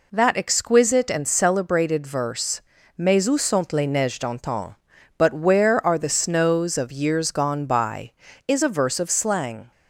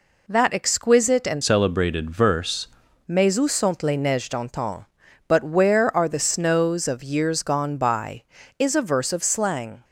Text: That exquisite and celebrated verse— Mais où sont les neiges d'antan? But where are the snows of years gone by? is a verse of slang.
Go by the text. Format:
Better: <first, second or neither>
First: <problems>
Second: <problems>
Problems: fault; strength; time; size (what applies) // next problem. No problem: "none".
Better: first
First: none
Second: changes voice from "celebrated" to "verse"; from 1.4 to 2.6 s; 1.2 s long